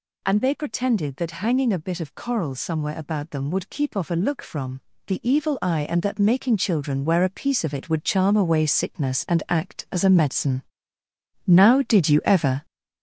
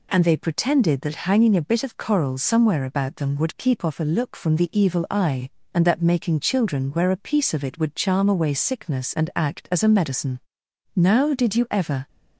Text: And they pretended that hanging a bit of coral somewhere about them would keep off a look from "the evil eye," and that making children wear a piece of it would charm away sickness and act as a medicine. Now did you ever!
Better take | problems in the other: second | gets louder; noticeable; throughout; 5.5 dB // pauses between "from" and "the"; slight; at 4.8 s; 0.26 s long

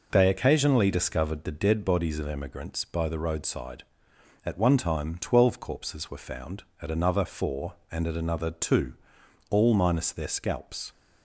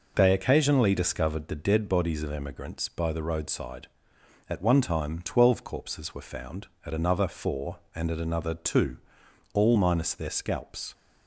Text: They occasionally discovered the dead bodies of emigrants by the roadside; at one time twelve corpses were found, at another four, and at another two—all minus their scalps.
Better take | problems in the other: neither | none

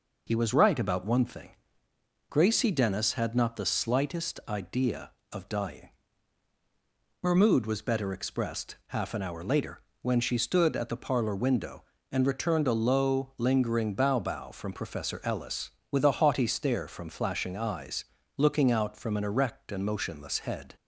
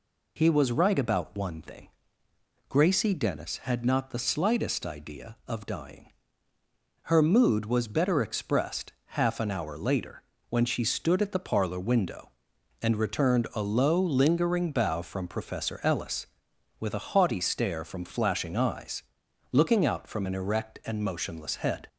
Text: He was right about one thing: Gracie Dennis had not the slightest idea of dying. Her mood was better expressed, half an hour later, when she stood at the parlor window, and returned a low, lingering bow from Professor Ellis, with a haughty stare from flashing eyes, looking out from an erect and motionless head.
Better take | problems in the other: second | says "bow" twice; at 14.1 s

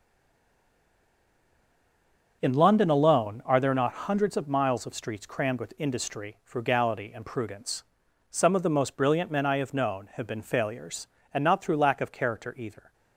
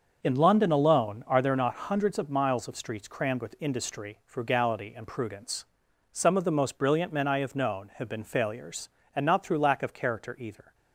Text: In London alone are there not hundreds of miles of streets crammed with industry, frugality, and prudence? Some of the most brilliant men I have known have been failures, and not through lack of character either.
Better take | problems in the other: second | stays silent before the first word; until 2.4 s; 2.4 s long // starts louder than the rest; until 3.4 s; 6.5 dB; also in the second

